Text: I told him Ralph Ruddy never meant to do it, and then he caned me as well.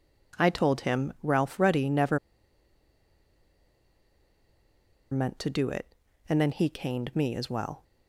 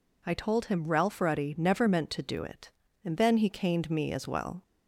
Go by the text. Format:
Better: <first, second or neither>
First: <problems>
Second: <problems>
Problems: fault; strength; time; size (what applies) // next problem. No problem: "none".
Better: second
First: pauses between "never" and "meant"; strong; at 2.1 s; 2.9 s long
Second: none